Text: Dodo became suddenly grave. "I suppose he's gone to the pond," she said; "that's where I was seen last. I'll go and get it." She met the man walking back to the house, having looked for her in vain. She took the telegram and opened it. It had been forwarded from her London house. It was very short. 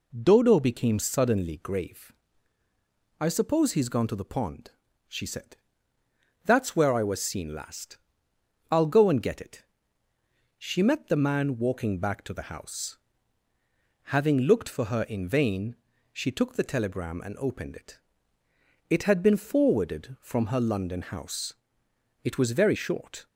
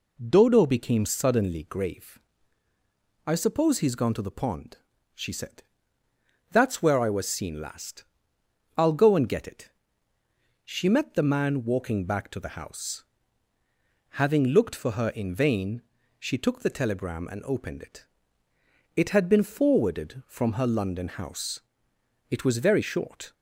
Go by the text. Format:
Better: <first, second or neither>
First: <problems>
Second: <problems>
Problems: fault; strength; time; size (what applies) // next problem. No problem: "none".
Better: neither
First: none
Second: none